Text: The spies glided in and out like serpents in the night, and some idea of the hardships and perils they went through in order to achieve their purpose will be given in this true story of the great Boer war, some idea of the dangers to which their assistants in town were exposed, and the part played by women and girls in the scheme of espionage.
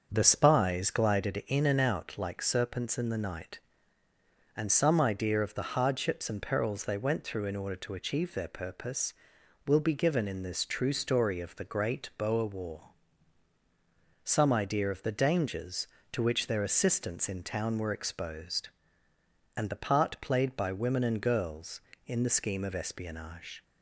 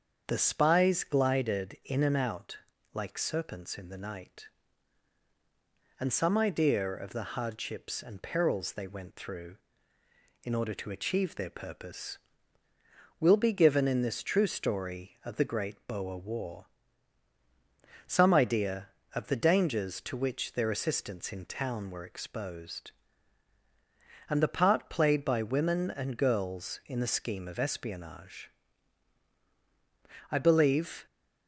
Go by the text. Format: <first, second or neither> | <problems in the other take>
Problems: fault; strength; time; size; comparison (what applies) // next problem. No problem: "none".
first | starts louder than the rest; strong; until 1.3 s; 7 dB; also in the first // pauses between "out" and "like"; slight; at 2.5 s; 0.36 s long // goes on to say "I believe"; noticeable; from 30.3 s on; 0.74 s long